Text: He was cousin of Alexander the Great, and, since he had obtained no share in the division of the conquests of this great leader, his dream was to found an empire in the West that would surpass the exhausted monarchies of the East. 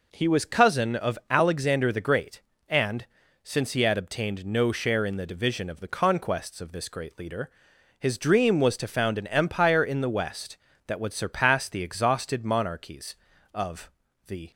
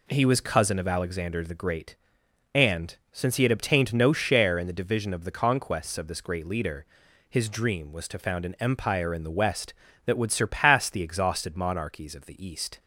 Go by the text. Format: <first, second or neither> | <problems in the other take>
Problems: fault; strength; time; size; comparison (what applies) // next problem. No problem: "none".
second | pauses between "of" and "the"; at 13.8 s; 0.38 s long // stops before "East"; at 14.5 s